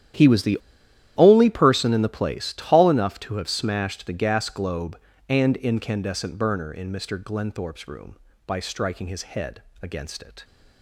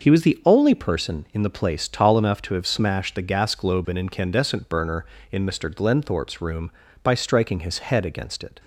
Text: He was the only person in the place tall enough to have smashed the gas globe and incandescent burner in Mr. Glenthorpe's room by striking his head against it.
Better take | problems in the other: second | starts louder than the rest; strong; until 1.7 s; 11.5 dB; noticeable in the second // pauses between "the" and "only"; noticeable; at 0.5 s; 0.61 s long // pauses between "head" and "against"; slight; at 9.6 s; 0.18 s long

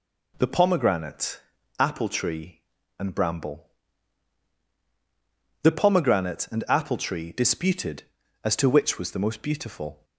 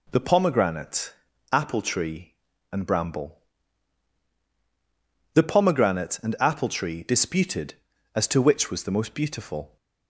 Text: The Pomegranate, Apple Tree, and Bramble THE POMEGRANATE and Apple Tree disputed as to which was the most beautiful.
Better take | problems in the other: neither | pauses between "Bramble" and "THE"; strong; the same in both

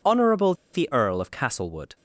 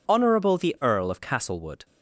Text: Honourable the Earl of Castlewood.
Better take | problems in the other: second | pauses between "Honourable" and "the"; slight; at 0.5 s; 0.19 s long

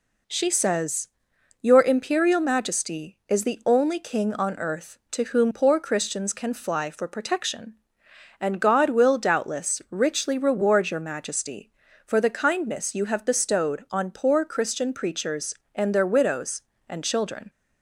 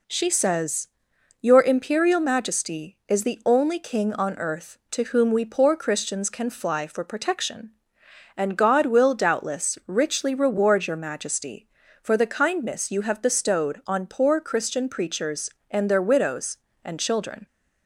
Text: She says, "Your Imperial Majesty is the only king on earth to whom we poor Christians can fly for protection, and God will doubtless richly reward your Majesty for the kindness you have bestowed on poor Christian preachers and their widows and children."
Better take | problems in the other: second | skips "we"; at 5.5 s

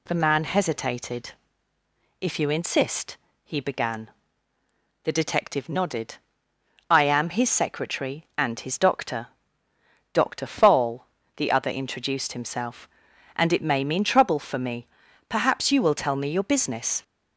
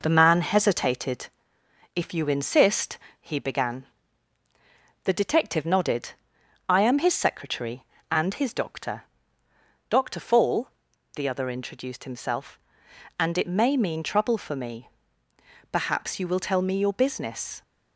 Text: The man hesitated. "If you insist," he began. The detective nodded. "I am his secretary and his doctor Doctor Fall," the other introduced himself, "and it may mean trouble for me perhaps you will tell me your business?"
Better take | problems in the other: first | gets quieter; slight; throughout; 3 dB // pauses between "doctor" and "Doctor"; noticeable; at 9.0 s; 0.86 s long; noticeable in the first // pauses between "me" and "perhaps"; noticeable; at 14.8 s; 0.82 s long; also in the first

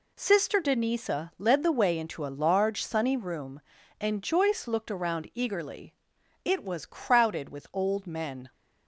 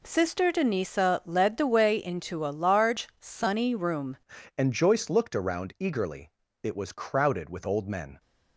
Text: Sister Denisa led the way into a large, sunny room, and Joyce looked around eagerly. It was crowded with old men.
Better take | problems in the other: first | changes voice at "and"; from 4.5 s on; 3.6 s long

